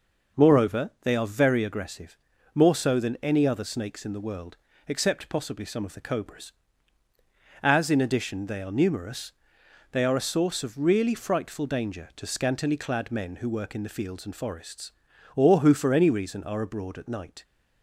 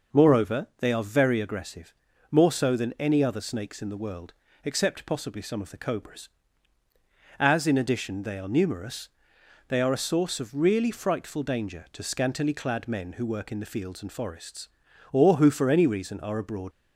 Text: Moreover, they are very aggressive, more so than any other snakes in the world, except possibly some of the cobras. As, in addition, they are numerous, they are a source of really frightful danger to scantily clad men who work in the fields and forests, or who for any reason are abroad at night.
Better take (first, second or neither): first